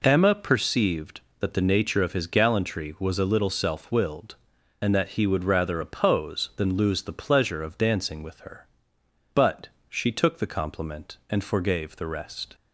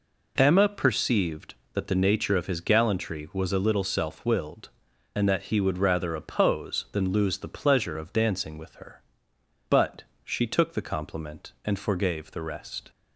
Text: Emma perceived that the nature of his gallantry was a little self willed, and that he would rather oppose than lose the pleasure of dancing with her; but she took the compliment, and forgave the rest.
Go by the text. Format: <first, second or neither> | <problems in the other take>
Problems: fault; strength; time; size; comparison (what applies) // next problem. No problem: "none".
neither | pauses between "but" and "she"; slight; the same in both